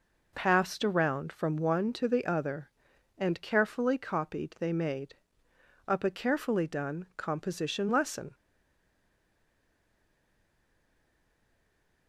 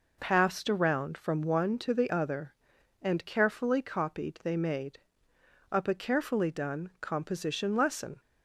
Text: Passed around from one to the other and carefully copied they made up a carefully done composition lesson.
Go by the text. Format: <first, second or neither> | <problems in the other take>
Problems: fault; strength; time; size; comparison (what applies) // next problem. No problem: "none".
second | pauses between "made" and "up"; noticeable; at 5.1 s; 0.74 s long; noticeable in the second // stays silent after the last word; strong; from 8.3 s on; 3.7 s long